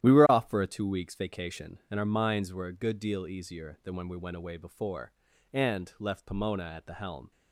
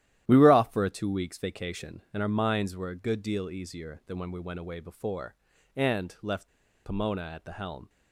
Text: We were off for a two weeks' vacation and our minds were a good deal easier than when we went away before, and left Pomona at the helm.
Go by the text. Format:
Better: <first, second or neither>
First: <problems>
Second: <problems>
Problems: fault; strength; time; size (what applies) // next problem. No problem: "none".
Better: first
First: starts louder than the rest; strong; until 1.0 s; 12 dB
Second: starts louder than the rest; strong; until 1.2 s; 12.5 dB // pauses between "left" and "Pomona"; at 6.4 s; 0.37 s long